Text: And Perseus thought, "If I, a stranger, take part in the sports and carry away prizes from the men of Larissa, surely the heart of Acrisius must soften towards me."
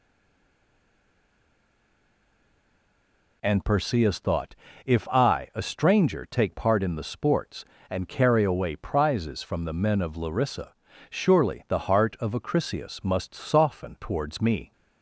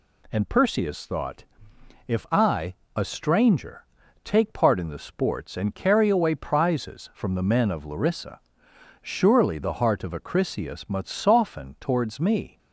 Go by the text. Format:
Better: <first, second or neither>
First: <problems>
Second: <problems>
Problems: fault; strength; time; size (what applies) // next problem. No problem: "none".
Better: second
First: stays silent before the first word; strong; until 3.4 s; 3.4 s long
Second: none